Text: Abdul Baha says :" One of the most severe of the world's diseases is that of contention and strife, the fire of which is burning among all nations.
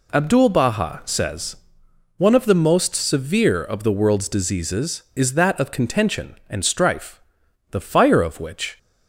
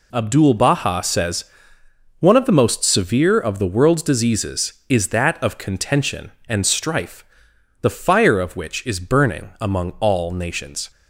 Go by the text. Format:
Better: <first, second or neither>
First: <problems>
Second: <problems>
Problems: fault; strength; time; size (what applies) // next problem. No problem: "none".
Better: second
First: stops before "is burning among all nations"; at 8.7 s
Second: none